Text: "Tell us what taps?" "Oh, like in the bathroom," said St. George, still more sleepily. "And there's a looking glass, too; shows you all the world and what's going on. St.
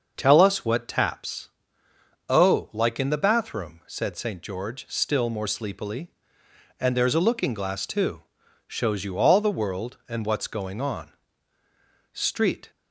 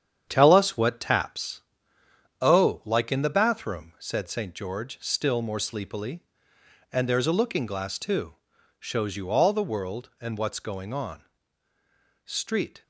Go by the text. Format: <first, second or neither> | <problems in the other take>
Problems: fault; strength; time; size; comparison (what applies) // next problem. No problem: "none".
first | gets quieter; throughout; 6.5 dB // starts louder than the rest; strong; until 1.2 s; 8.5 dB; also in the first